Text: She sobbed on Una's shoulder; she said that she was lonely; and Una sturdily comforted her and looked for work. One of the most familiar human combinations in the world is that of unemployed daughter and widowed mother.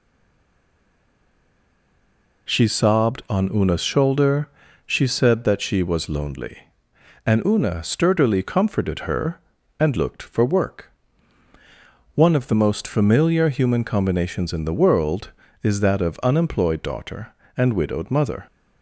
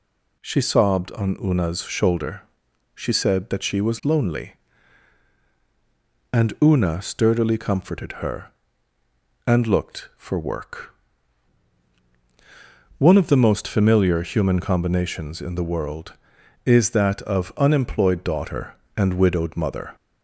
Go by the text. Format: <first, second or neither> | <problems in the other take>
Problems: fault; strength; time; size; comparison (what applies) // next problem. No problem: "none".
second | stays silent before the first word; until 2.4 s; 2.4 s long